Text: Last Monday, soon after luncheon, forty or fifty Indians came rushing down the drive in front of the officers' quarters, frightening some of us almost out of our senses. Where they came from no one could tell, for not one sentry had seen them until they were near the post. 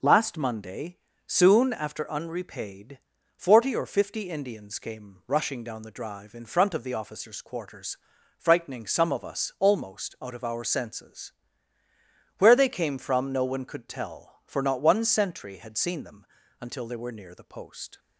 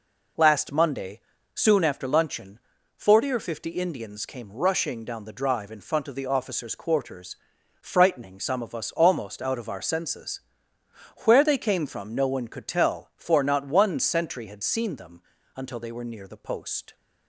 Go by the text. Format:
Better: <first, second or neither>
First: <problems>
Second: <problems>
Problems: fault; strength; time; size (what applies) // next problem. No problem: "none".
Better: second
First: says "unrepaid" for "luncheon"; at 2.0 s // pauses between "them" and "until"; slight; at 16.2 s; 0.36 s long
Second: pauses between "them" and "until"; slight; at 15.2 s; 0.34 s long